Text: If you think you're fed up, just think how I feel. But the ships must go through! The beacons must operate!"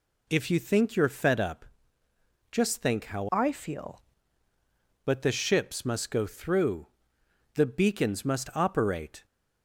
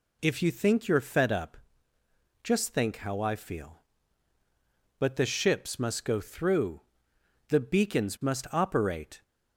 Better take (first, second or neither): second